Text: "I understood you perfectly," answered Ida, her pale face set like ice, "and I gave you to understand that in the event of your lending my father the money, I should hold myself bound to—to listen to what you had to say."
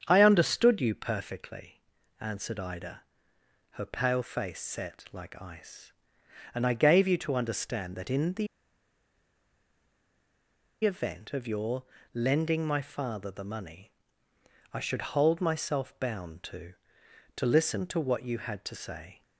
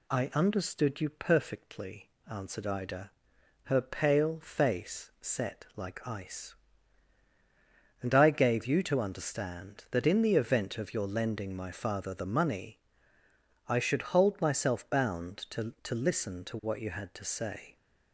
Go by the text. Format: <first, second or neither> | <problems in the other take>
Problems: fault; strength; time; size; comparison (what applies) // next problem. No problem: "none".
second | starts louder than the rest; strong; until 1.0 s; 8 dB // pauses between "the" and "event"; strong; at 8.4 s; 2.3 s long // pauses between "your" and "lending"; slight; at 11.8 s; 0.28 s long